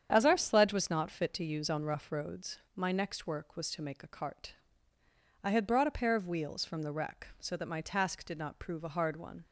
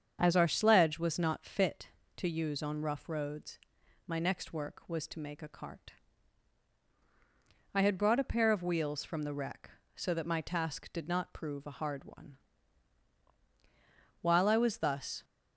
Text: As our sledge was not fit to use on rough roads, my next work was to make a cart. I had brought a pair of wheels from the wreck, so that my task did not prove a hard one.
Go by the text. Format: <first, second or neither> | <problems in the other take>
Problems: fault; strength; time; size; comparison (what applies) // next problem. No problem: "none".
first | starts louder than the rest; strong; until 1.2 s; 7.5 dB; strong in the first // goes on to say "While I was thus"; noticeable; from 14.2 s on; 1.0 s long